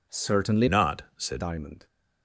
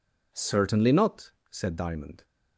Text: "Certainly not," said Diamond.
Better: second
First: changes voice from "not" to "said"; from 0.6 to 1.4 s; 0.8 s long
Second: none

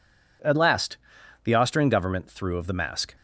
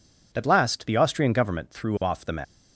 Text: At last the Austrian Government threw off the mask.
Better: second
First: pauses between "last" and "the"; noticeable; at 0.9 s; 0.48 s long // says "of" for "off"; at 2.5 s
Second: none

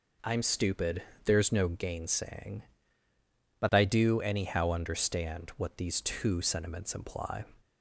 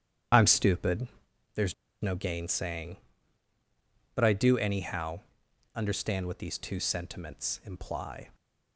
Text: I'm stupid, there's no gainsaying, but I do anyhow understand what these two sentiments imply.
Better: first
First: none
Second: starts louder than the rest; strong; until 2.0 s; 9.5 dB // pauses between "there's" and "no"; slight; at 1.7 s; 0.28 s long // pauses between "anyhow" and "understand"; noticeable; at 5.2 s; 0.54 s long

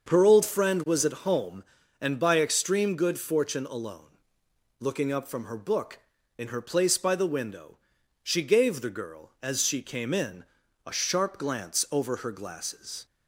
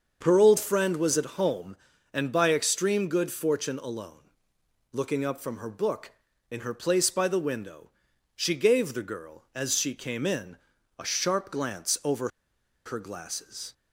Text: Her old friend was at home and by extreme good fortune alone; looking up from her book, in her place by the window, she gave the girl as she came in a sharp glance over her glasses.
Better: first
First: starts louder than the rest; until 1.1 s; 6.5 dB // pauses between "in" and "a"; at 10.4 s; 0.42 s long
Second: starts louder than the rest; until 1.2 s; 6.5 dB // pauses between "in" and "a"; at 10.5 s; 0.42 s long // pauses between "over" and "her"; noticeable; at 12.2 s; 0.56 s long

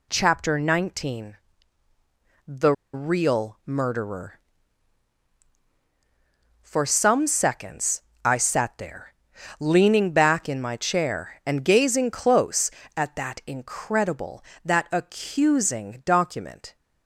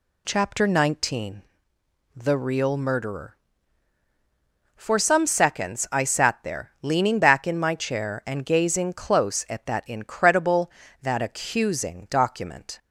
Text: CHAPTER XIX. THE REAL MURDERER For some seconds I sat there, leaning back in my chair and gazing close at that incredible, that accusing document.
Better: second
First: pauses between "THE" and "REAL"; slight; at 2.7 s; 0.21 s long // pauses between "seconds" and "I"; slight; at 8.0 s; 0.24 s long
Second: none

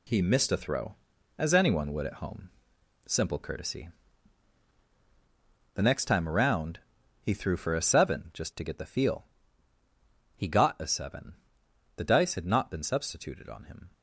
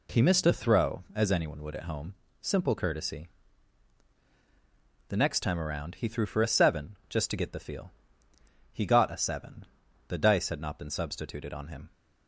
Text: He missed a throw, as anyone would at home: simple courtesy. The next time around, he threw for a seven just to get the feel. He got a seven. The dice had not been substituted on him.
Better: second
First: gets quieter; strong; throughout; 8.5 dB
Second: none

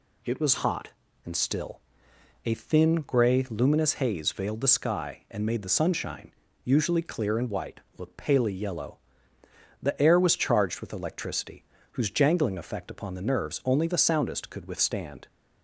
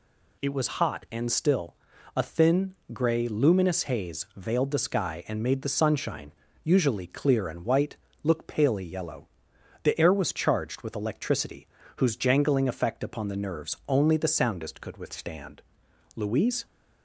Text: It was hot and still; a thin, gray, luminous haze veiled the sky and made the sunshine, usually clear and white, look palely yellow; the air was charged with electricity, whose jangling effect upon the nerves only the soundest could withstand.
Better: first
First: none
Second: goes on to say "Louise"; from 16.1 s on; 0.52 s long

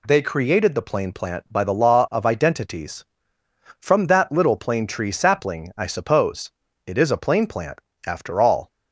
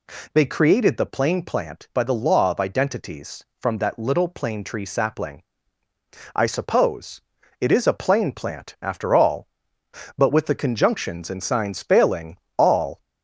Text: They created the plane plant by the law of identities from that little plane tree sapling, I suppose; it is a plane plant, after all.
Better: first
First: none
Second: goes on to say "But with the conjunctions and signs failing all"; strong; from 10.1 s on; 2.8 s long

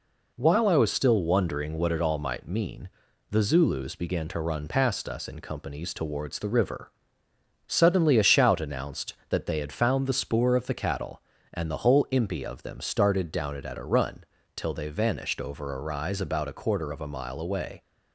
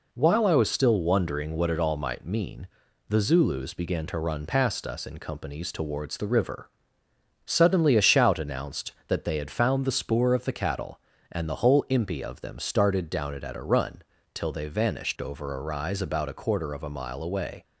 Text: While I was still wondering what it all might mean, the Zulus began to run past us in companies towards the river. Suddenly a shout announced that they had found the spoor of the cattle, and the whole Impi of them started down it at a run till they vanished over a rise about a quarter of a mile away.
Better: neither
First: pauses between "run" and "till"; slight; at 14.2 s; 0.32 s long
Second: pauses between "run" and "till"; slight; at 14.0 s; 0.32 s long

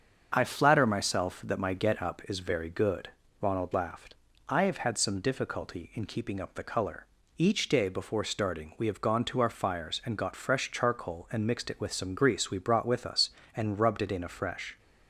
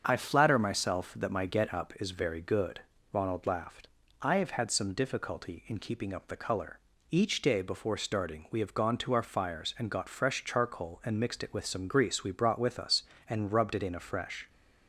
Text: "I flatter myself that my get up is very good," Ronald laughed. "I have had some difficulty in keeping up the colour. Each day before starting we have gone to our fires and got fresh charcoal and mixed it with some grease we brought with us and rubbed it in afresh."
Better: neither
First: starts louder than the rest; until 1.3 s; 7 dB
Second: starts louder than the rest; until 1.0 s; 7 dB

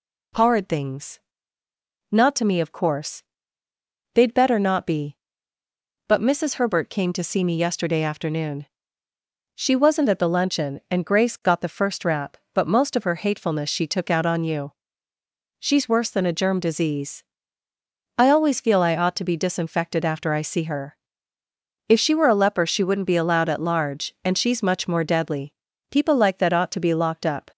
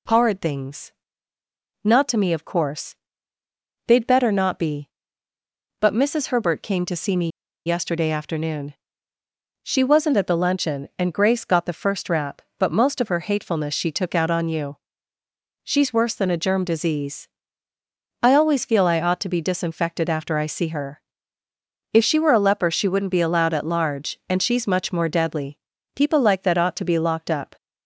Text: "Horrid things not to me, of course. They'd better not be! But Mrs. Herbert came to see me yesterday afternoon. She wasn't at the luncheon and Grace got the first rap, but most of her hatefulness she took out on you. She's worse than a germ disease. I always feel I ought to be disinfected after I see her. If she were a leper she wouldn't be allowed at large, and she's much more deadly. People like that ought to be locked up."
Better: first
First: pauses between "things" and "not"; noticeable; at 1.1 s; 0.90 s long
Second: pauses between "things" and "not"; noticeable; at 0.9 s; 0.90 s long // pauses between "me" and "yesterday"; at 7.2 s; 0.37 s long

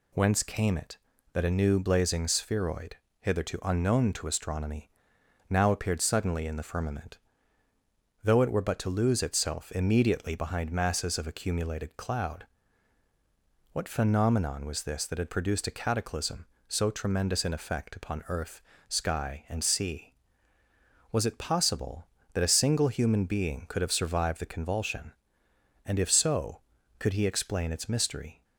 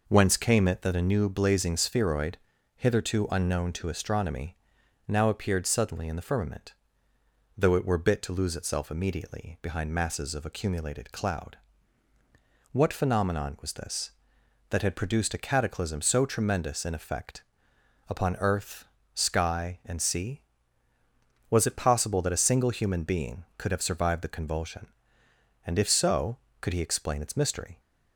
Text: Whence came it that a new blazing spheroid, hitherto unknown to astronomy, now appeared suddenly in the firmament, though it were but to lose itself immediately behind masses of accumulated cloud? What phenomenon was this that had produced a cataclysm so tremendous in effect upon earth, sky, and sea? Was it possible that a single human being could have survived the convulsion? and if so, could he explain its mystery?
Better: first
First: none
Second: says "bit" for "but"; at 7.9 s // pauses between "effect" and "upon"; noticeable; at 17.4 s; 0.66 s long

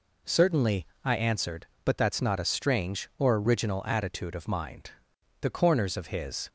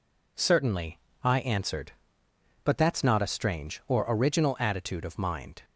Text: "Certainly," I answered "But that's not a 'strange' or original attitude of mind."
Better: second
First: goes on to say "The corners of his"; noticeable; from 5.4 s on; 1.0 s long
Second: none

